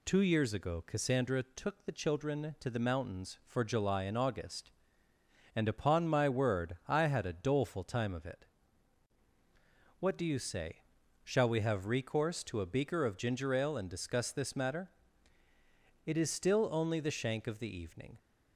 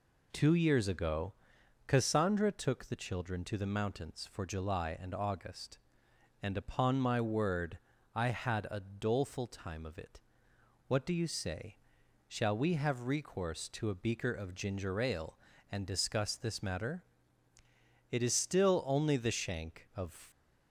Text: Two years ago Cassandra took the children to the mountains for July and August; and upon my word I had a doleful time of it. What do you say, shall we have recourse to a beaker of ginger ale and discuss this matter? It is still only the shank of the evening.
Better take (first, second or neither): first